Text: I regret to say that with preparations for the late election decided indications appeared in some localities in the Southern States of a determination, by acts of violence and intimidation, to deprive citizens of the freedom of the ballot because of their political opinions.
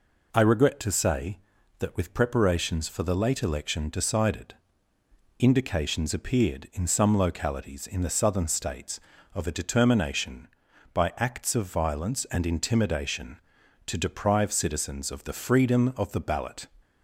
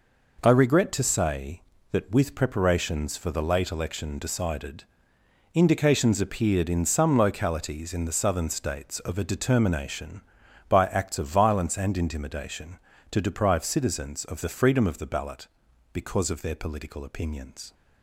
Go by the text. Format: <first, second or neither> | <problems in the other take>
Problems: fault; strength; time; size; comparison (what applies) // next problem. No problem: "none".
second | pauses between "decided" and "indications"; noticeable; at 4.5 s; 0.86 s long; noticeable in the second // stops before "because of their political opinions"; at 16.8 s